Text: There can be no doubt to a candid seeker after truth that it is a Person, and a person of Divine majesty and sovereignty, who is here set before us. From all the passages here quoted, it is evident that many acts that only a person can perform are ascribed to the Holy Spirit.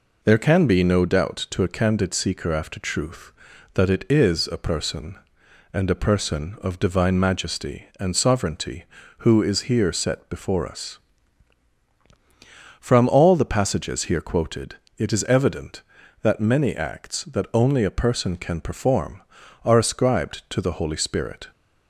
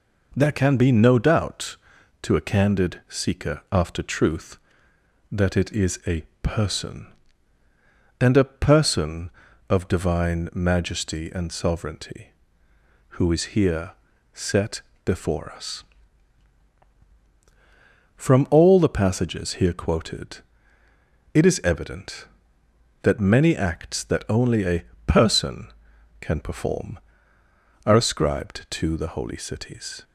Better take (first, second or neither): first